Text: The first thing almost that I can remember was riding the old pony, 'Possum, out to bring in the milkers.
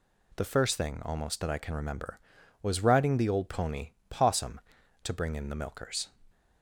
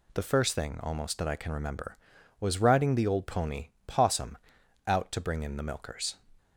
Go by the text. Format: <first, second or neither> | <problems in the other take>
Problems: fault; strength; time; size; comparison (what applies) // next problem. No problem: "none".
second | skips "out"; at 4.8 s